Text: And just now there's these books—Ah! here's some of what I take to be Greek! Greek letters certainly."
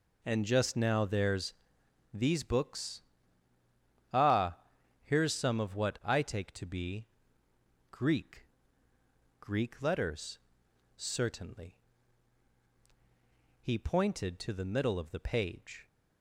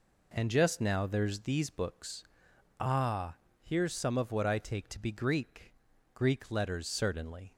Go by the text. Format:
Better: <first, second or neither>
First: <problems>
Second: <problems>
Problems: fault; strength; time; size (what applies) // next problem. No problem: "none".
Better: second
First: pauses between "there's" and "these"; noticeable; at 1.5 s; 0.60 s long // pauses between "be" and "Greek"; noticeable; at 7.0 s; 0.86 s long // pauses between "letters" and "certainly"; noticeable; at 10.3 s; 0.56 s long // goes on to say "He pointed to the middle of the page"; strong; from 13.6 s on; 2.2 s long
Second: none